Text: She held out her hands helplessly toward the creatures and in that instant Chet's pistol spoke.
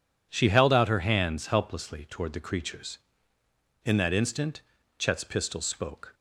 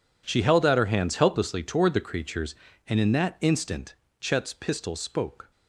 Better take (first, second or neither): second